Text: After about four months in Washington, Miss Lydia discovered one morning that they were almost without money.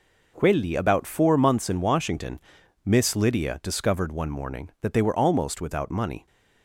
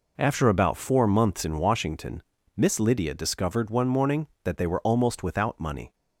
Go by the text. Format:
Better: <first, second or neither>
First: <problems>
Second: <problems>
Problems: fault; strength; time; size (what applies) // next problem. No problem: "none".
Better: second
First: says "Quelli" for "After"; at 0.3 s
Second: none